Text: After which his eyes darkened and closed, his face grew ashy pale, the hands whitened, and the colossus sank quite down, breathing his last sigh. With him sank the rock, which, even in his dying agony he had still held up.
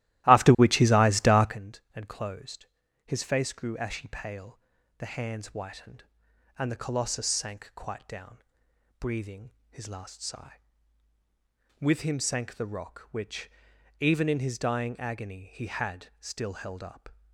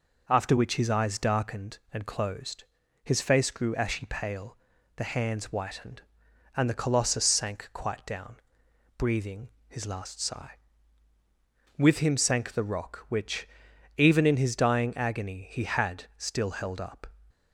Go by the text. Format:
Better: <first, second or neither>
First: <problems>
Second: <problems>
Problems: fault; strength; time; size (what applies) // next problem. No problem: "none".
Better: second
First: starts louder than the rest; strong; until 1.6 s; 16 dB // pauses between "breathing" and "his"; slight; at 9.5 s; 0.20 s long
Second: pauses between "breathing" and "his"; slight; at 9.4 s; 0.20 s long